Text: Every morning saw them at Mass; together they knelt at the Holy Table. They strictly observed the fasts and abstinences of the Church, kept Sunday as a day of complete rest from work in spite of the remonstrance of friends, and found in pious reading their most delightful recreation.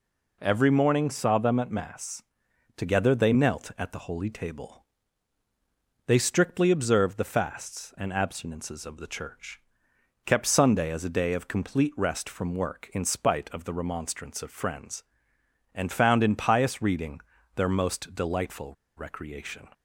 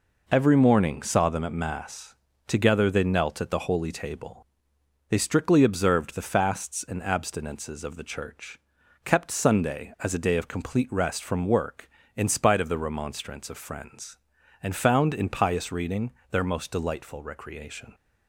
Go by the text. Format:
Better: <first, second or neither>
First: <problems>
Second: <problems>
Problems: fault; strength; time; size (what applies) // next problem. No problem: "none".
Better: second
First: pauses between "reading" and "their"; slight; at 17.2 s; 0.34 s long // pauses between "delightful" and "recreation"; slight; at 18.7 s; 0.22 s long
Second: pauses between "reading" and "their"; slight; at 16.1 s; 0.18 s long